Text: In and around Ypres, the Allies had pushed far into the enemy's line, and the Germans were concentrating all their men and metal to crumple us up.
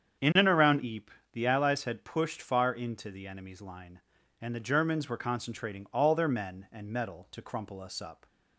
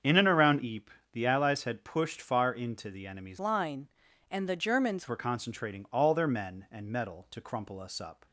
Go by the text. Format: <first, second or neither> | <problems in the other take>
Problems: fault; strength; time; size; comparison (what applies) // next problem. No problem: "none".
first | starts louder than the rest; strong; until 1.1 s; 7.5 dB; strong in the first // changes voice from "line" to "Germans"; from 3.3 to 5.0 s; 1.7 s long